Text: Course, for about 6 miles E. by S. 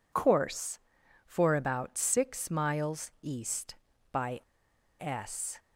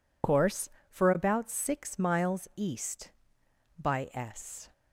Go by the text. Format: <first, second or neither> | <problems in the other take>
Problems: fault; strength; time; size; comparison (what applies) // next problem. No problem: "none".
second | pauses between "by" and "S"; noticeable; at 4.3 s; 0.61 s long